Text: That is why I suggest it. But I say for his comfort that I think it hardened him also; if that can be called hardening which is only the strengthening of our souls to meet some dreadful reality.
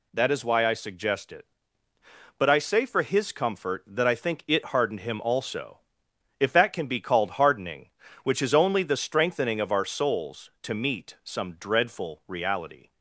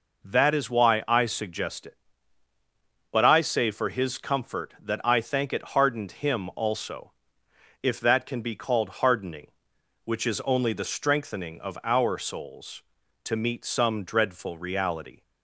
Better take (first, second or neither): first